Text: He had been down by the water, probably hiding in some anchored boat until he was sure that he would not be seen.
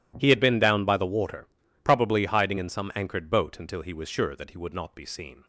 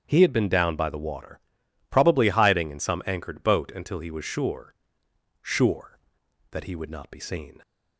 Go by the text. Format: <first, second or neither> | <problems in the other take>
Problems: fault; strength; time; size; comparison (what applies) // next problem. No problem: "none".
first | starts louder than the rest; strong; until 1.0 s; 8 dB // says "sure" twice; at 5.4 s